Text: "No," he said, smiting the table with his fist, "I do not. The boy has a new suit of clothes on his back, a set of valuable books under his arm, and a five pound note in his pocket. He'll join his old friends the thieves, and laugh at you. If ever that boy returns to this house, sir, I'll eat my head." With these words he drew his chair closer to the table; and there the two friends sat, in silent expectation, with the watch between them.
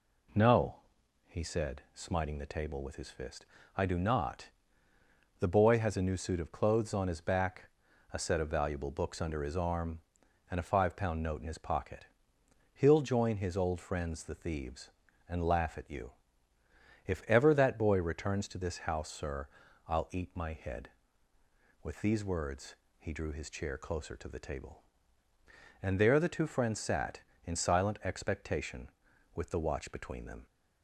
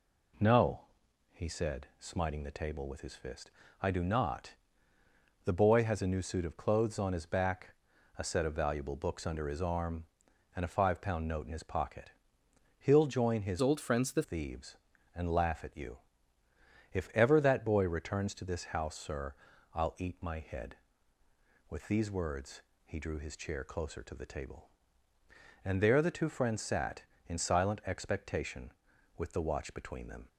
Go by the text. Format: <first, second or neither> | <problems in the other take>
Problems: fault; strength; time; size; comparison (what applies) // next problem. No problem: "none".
first | changes voice from "old" to "the"; from 13.6 to 14.2 s; 0.6 s long // pauses between "words" and "he"; slight; at 22.6 s; 0.22 s long; slight in the first